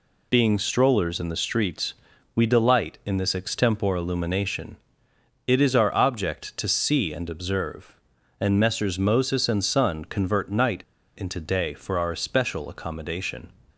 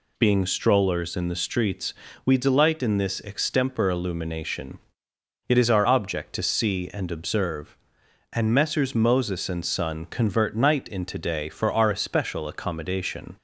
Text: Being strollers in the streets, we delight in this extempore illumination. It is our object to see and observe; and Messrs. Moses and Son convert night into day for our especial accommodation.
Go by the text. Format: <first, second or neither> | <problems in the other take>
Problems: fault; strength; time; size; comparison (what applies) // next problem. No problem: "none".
second | pauses between "night" and "into"; at 10.8 s; 0.37 s long